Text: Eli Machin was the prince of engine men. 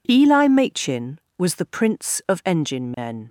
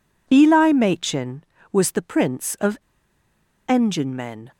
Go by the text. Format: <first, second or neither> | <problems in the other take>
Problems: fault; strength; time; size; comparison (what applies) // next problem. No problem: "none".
first | pauses between "of" and "engine"; noticeable; at 2.7 s; 0.89 s long